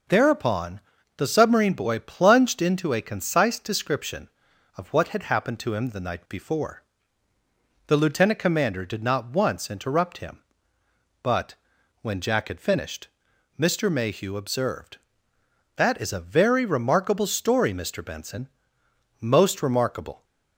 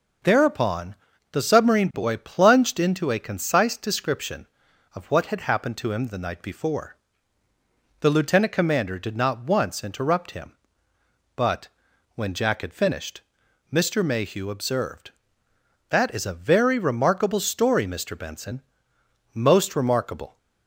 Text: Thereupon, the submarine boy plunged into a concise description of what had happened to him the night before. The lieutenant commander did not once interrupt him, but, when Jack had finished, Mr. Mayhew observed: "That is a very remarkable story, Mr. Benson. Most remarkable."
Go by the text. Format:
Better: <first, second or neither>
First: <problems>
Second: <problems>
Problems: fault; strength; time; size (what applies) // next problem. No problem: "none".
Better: neither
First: none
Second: none